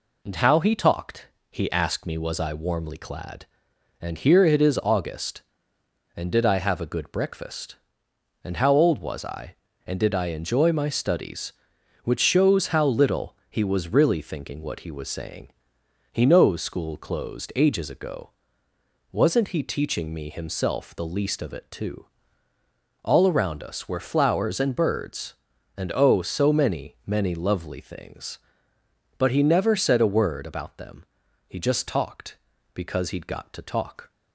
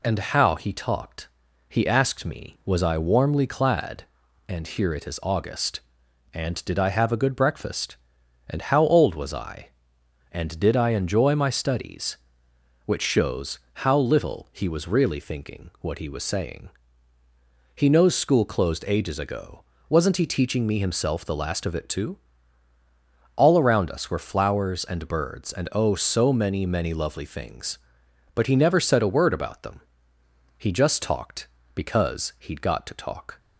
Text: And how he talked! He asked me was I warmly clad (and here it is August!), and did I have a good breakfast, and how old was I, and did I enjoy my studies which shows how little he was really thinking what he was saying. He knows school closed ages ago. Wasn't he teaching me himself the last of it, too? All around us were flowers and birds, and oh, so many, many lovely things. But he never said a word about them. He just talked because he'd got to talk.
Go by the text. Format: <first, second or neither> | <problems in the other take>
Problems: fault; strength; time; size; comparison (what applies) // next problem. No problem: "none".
second | says "least" for "last"; at 21.0 s